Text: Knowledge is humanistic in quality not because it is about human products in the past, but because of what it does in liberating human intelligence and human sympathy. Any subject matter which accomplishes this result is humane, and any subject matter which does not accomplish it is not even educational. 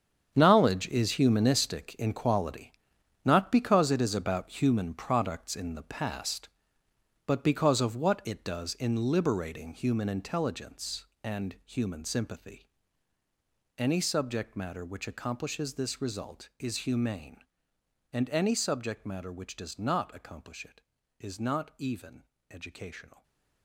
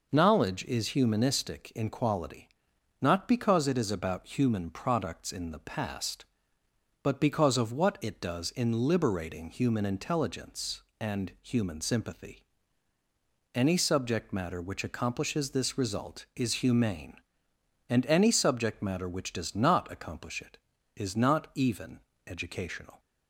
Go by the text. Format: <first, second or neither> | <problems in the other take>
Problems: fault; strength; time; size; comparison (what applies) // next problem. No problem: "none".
second | gets quieter; strong; throughout; 12.5 dB // pauses between "quality" and "not"; noticeable; at 2.7 s; 0.54 s long; noticeable in the second // pauses between "even" and "educational"; slight; at 22.2 s; 0.26 s long; slight in the second // stays silent after the last word; slight; from 23.1 s on; 0.5 s long